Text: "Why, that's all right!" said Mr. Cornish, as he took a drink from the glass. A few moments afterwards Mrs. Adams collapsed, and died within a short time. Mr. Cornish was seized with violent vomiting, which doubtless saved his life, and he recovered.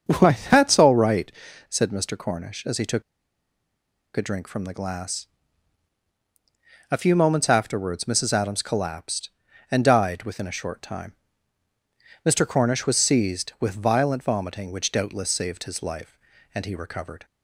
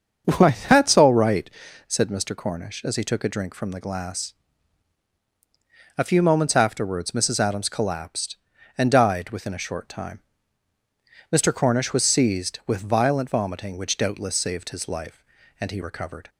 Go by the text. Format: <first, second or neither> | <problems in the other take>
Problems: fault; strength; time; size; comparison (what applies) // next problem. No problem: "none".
second | starts louder than the rest; until 1.2 s; 7 dB; also in the second // pauses between "took" and "a"; at 3.0 s; 1.1 s long